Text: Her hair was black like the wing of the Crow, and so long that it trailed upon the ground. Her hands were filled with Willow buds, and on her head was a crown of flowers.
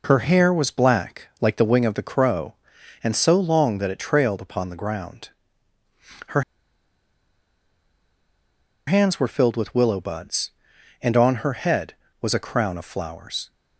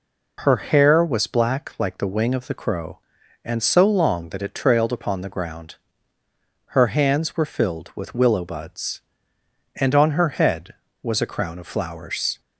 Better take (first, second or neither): second